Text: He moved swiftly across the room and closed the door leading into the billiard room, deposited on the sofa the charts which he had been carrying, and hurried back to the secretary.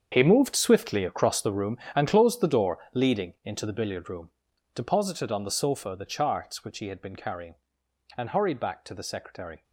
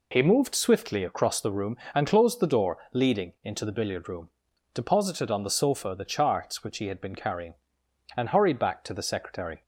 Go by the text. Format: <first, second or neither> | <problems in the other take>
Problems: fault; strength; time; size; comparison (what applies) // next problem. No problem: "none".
second | gets quieter; strong; throughout; 14 dB // pauses between "door" and "leading"; slight; at 2.7 s; 0.16 s long; slight in the second